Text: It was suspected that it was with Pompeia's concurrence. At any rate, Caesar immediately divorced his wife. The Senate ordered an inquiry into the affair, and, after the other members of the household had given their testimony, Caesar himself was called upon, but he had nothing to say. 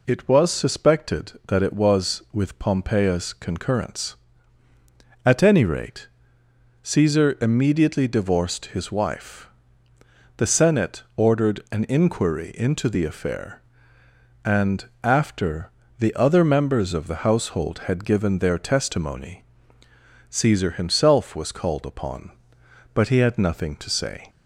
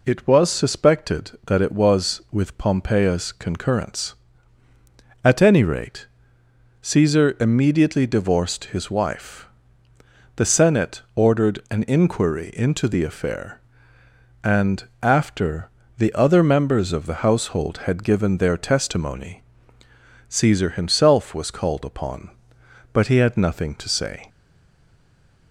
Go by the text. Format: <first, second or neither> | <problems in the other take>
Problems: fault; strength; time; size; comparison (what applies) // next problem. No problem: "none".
first | pauses between "Senate" and "ordered"; slight; at 10.9 s; 0.16 s long; slight in the first // pauses between "after" and "the"; slight; at 15.6 s; 0.26 s long; slight in the first // stays silent after the last word; noticeable; from 24.2 s on; 1.3 s long